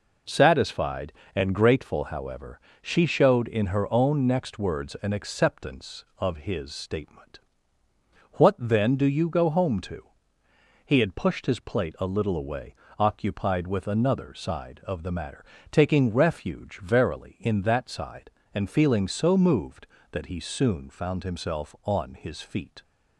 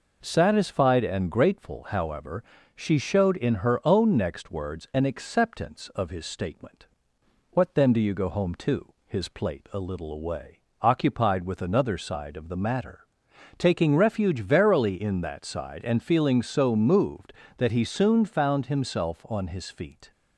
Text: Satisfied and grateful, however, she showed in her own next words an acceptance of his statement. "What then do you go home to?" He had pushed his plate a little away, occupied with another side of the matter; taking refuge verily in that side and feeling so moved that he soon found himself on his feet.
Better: first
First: none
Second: skips "He had pushed"; at 9.0 s

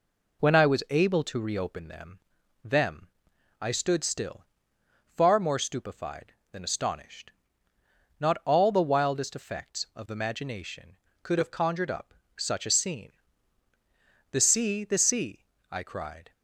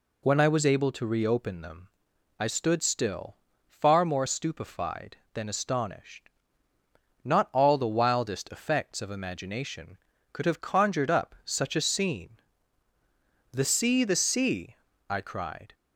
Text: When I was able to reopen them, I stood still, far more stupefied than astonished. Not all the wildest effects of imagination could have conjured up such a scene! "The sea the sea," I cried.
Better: second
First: says "them" twice; at 2.6 s // pauses between "up" and "such"; slight; at 12.1 s; 0.24 s long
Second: none

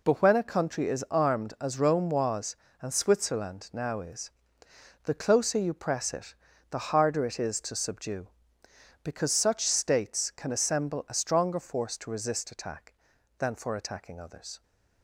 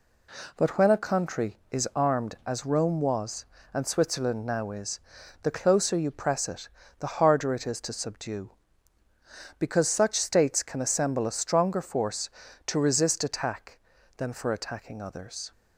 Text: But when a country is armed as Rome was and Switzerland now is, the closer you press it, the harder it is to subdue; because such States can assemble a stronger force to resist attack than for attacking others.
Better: neither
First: none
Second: none

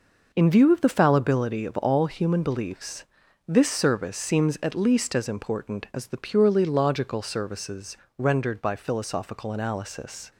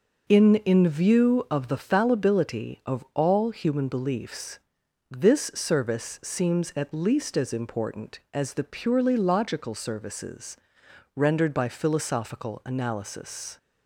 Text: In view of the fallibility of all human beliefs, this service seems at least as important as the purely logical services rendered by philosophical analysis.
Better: first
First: pauses between "services" and "rendered"; slight; at 7.9 s; 0.20 s long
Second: says "In" twice; at 0.6 s // pauses between "services" and "rendered"; noticeable; at 10.5 s; 0.58 s long

